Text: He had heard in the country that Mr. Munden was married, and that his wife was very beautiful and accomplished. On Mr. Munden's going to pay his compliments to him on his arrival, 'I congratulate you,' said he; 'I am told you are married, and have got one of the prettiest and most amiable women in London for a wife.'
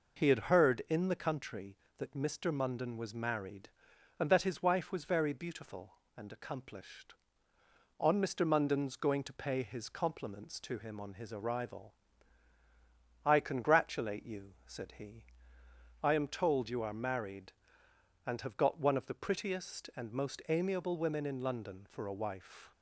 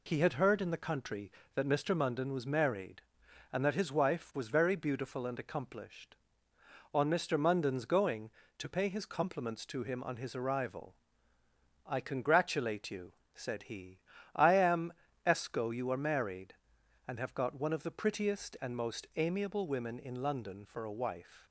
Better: first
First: none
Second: says "esco" for "told"; at 15.2 s

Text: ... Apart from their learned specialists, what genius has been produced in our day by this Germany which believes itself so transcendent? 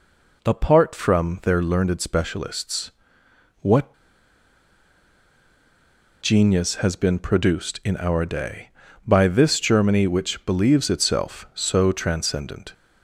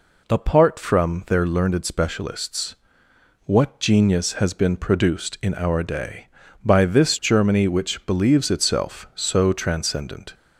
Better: second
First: pauses between "what" and "genius"; strong; at 3.9 s; 2.2 s long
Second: none

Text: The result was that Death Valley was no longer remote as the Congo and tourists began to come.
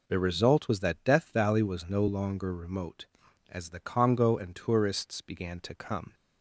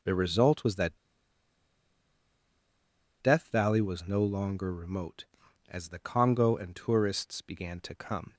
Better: first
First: none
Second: pauses between "that" and "Death"; strong; at 0.9 s; 2.2 s long

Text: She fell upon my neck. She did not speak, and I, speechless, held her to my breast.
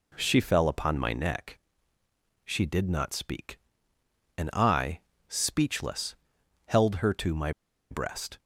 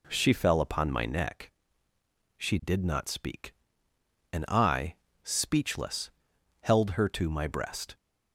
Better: second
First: pauses between "my" and "breast"; at 7.5 s; 0.39 s long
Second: none

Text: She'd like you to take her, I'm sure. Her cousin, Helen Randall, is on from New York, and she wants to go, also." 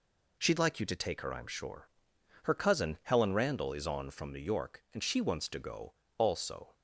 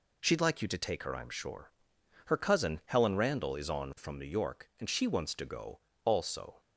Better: neither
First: none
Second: none

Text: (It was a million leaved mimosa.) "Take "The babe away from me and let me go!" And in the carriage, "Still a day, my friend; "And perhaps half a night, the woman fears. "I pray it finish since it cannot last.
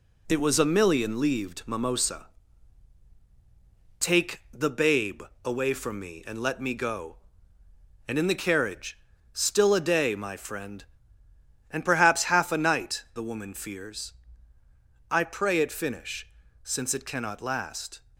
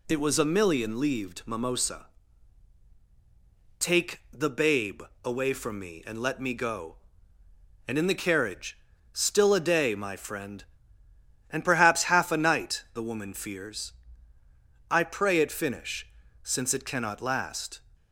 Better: second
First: gets quieter; noticeable; throughout; 4 dB // pauses between "babe" and "away"; slight; at 5.2 s; 0.22 s long // pauses between "finish" and "since"; slight; at 16.2 s; 0.36 s long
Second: pauses between "babe" and "away"; slight; at 5.0 s; 0.22 s long // pauses between "finish" and "since"; slight; at 16.0 s; 0.36 s long

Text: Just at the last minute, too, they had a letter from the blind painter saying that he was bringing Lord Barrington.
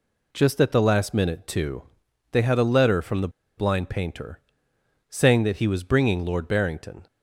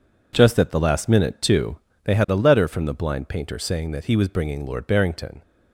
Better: second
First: pauses between "the" and "blind"; slight; at 3.2 s; 0.28 s long // pauses between "painter" and "saying"; noticeable; at 4.4 s; 0.68 s long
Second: none

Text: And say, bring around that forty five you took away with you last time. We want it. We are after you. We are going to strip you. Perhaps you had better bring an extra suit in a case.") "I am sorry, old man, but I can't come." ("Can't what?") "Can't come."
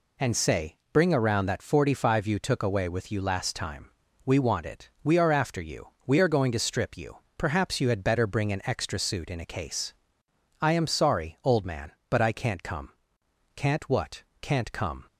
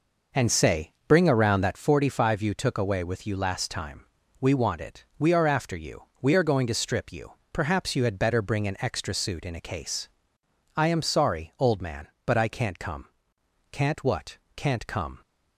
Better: first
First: none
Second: starts louder than the rest; noticeable; until 2.0 s; 5 dB

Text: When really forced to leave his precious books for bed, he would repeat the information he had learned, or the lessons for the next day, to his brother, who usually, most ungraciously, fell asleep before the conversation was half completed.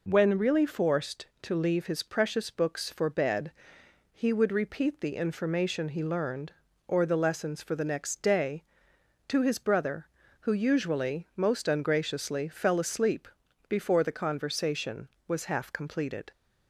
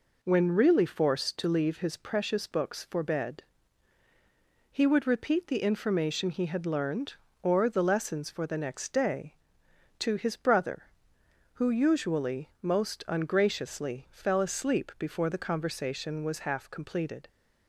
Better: second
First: skips "had"; at 6.0 s // pauses between "asleep" and "before"; at 13.2 s; 0.40 s long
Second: none

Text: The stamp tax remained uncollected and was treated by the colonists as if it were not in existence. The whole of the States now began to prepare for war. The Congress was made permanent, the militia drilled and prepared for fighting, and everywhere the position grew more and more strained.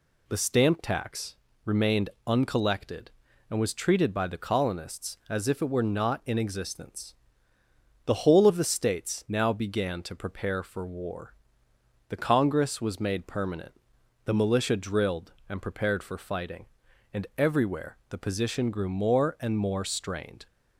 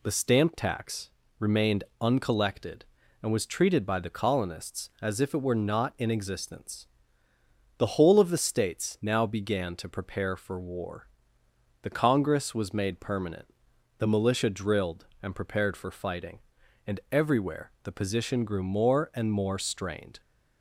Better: neither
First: pauses between "tax" and "remained"; slight; at 1.3 s; 0.28 s long // pauses between "remained" and "uncollected"; slight; at 2.0 s; 0.16 s long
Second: pauses between "tax" and "remained"; slight; at 1.1 s; 0.28 s long // pauses between "remained" and "uncollected"; slight; at 1.8 s; 0.16 s long

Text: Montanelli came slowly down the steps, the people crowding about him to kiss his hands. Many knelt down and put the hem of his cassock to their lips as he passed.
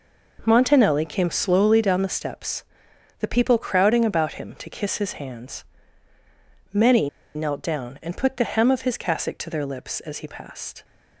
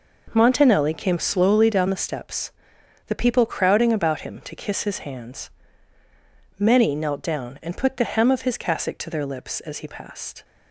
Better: second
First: pauses between "Many" and "knelt"; slight; at 7.0 s; 0.26 s long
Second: none

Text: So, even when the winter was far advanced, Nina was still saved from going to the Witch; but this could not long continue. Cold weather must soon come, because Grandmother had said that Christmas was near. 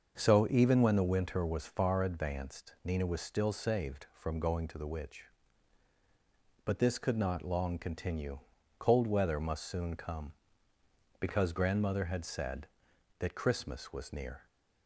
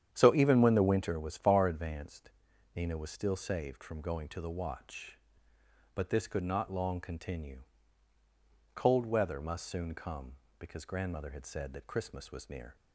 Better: first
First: starts louder than the rest; until 1.1 s; 6.5 dB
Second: starts louder than the rest; strong; until 1.1 s; 9.5 dB // says "Watch" for "Witch"; at 4.4 s

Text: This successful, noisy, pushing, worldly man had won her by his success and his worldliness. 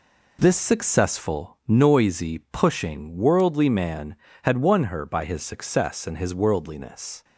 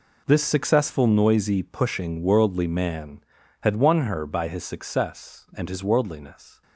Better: neither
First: none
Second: none

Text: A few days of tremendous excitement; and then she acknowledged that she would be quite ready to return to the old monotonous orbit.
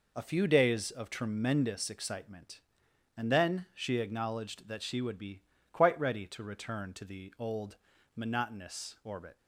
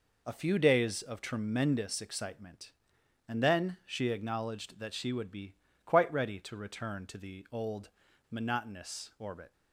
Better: neither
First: pauses between "be" and "quite"; slight; at 5.4 s; 0.32 s long // pauses between "old" and "monotonous"; at 7.7 s; 0.40 s long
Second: pauses between "be" and "quite"; slight; at 5.5 s; 0.32 s long // pauses between "old" and "monotonous"; at 7.8 s; 0.41 s long

